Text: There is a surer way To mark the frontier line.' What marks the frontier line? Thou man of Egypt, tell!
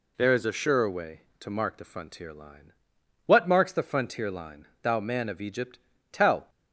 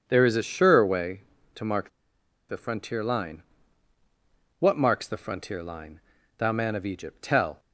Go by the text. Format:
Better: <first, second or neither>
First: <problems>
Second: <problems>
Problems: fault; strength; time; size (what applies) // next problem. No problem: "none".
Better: first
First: none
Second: starts louder than the rest; strong; until 1.0 s; 7.5 dB // pauses between "mark" and "the"; noticeable; at 1.8 s; 0.60 s long